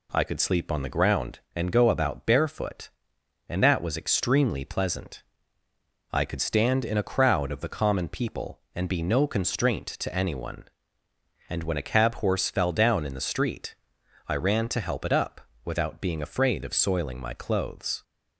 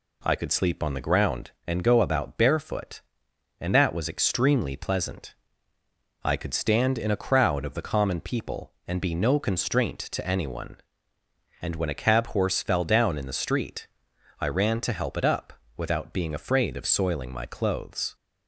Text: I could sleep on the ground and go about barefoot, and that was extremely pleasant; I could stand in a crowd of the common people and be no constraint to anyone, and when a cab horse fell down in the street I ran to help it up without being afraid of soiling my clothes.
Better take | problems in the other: neither | pauses between "street" and "I"; noticeable; the same in both // pauses between "up" and "without"; slight; the same in both

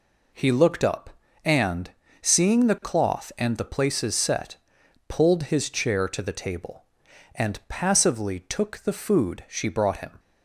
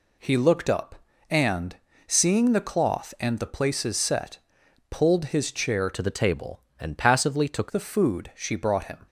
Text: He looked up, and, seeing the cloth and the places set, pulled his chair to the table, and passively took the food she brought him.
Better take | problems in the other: first | changes voice from "to" to "took"; from 5.9 to 7.7 s; 1.8 s long

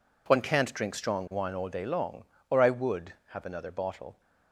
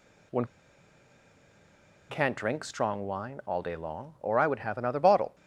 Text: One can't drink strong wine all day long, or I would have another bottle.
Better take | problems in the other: first | pauses between "One" and "can't"; strong; at 0.4 s; 1.6 s long

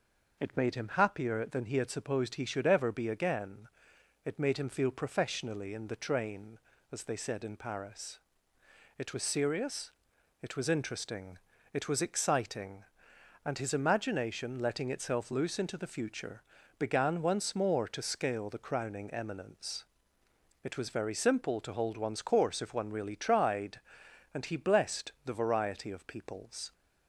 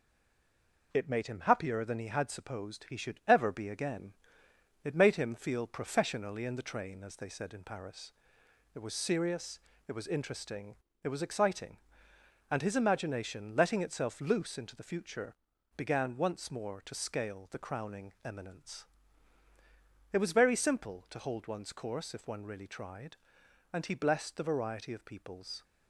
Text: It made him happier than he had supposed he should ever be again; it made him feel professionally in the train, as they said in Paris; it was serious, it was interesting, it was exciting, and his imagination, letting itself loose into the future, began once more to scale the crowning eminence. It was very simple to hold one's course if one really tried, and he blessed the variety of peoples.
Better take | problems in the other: first | stays silent before the first word; slight; until 0.9 s; 0.9 s long

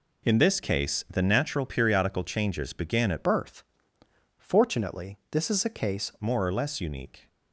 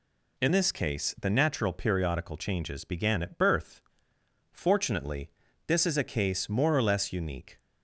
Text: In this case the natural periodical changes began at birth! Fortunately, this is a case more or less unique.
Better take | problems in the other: second | changes voice from "birth" to "case"; from 3.2 to 6.1 s; 2.9 s long

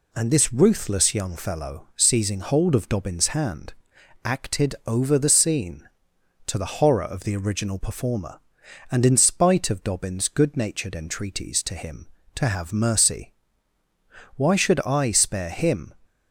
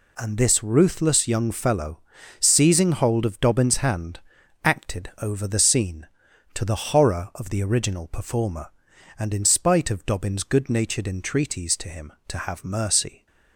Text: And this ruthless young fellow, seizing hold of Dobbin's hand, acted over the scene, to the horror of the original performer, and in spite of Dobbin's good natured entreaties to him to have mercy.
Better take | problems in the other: second | goes on to say "Why should I spare him"; from 14.3 s on; 1.5 s long

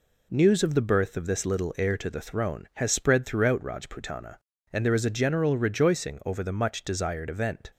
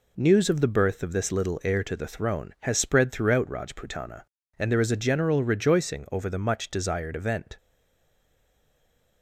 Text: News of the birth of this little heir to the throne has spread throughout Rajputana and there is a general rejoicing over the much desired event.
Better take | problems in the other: first | stays silent after the last word; noticeable; from 7.5 s on; 1.7 s long

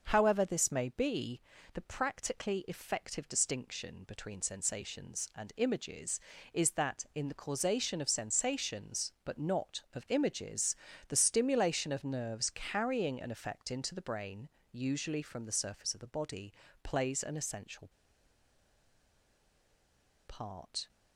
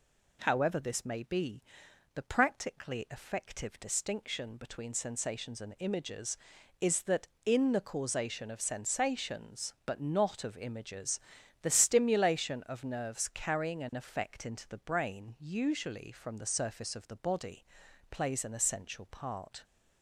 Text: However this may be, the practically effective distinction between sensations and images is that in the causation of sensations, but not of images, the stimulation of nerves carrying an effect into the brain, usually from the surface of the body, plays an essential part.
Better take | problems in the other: second | starts louder than the rest; until 1.0 s; 6 dB // pauses between "essential" and "part"; strong; at 17.8 s; 2.4 s long

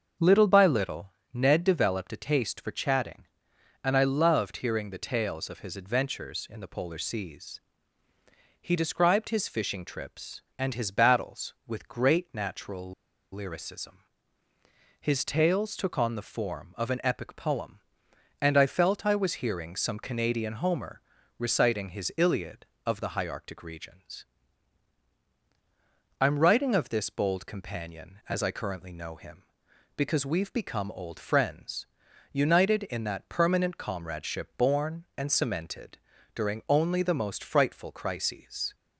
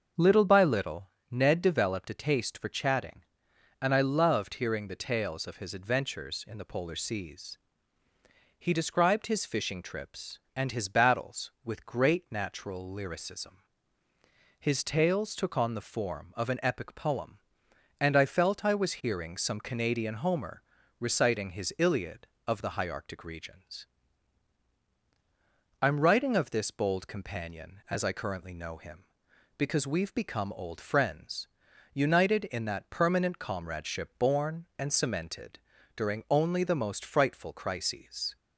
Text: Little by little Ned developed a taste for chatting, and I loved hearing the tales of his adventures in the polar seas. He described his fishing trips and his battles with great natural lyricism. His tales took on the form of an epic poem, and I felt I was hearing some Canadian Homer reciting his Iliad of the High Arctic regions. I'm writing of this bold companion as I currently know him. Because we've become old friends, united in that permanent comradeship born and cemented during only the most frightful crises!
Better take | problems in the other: second | starts louder than the rest; until 1.4 s; 6.5 dB; also in the second // pauses between "little" and "Ned"; slight; at 1.1 s; 0.20 s long; slight in the second // pauses between "natural" and "lyricism"; at 12.9 s; 0.40 s long // pauses between "Homer" and "reciting"; slight; at 21.0 s; 0.36 s long; slight in the second // pauses between "cemented" and "during"; at 35.9 s; 0.38 s long; also in the second

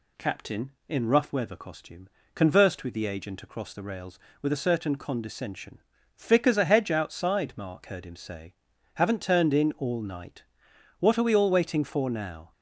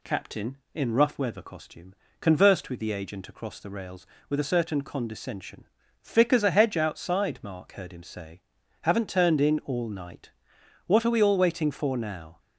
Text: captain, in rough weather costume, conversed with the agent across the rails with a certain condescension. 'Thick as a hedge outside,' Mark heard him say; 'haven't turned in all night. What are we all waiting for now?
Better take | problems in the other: neither | none

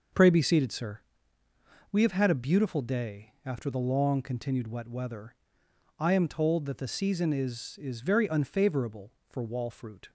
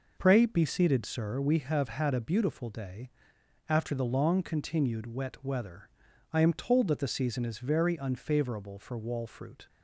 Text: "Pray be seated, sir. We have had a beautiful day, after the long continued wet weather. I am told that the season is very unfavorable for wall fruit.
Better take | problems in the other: second | says "is" twice; at 7.8 s

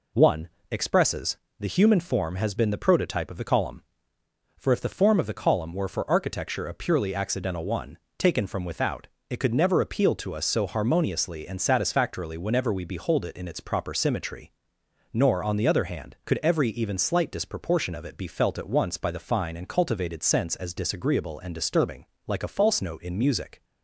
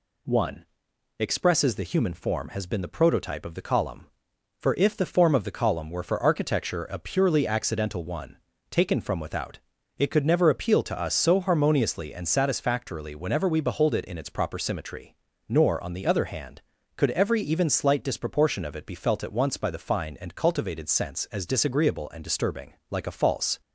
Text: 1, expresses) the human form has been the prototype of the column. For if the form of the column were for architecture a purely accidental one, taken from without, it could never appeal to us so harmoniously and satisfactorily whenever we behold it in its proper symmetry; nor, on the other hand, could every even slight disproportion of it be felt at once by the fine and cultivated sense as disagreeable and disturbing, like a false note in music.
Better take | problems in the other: first | stops before "note in music"; at 23.6 s

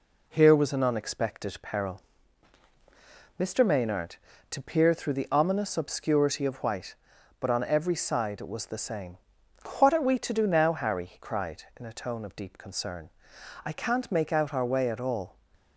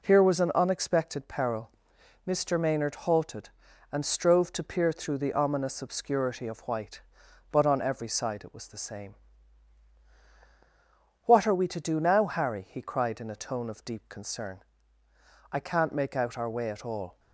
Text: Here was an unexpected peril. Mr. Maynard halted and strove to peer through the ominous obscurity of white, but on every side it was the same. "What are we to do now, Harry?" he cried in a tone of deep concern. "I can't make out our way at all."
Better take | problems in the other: second | skips "halted and strove"; at 4.3 s

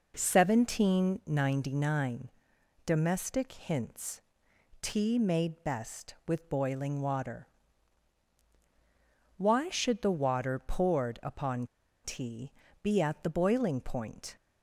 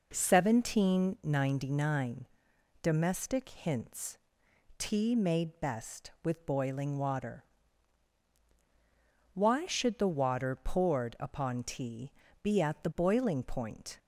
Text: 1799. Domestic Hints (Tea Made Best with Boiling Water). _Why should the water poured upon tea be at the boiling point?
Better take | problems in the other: second | pauses between "upon" and "tea"; at 11.6 s; 0.37 s long // pauses between "tea" and "be"; slight; at 12.5 s; 0.30 s long; slight in the second

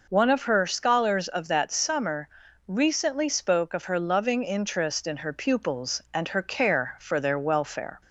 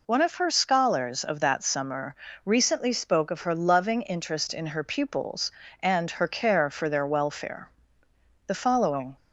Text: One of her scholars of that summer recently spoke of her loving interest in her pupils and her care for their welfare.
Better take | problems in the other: first | pauses between "summer" and "recently"; slight; at 2.1 s; 0.30 s long; also in the first // goes on to say "The following"; noticeable; from 8.4 s on; 0.70 s long

